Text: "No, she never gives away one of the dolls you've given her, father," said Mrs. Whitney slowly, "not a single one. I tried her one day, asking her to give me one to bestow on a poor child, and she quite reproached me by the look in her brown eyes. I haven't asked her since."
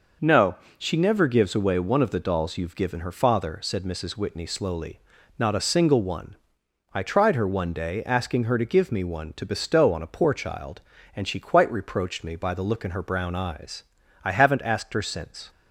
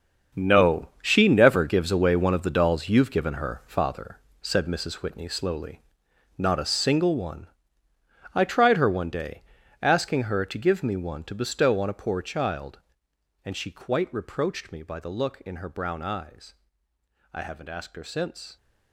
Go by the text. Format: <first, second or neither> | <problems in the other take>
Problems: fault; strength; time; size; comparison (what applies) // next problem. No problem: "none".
first | gets quieter; strong; throughout; 13 dB